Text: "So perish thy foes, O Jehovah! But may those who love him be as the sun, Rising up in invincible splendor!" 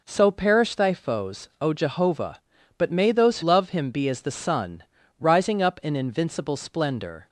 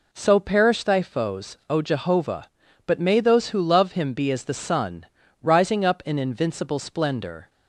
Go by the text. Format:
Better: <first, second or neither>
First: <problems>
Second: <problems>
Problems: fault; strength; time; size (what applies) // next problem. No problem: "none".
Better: second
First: skips "who"; at 3.4 s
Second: none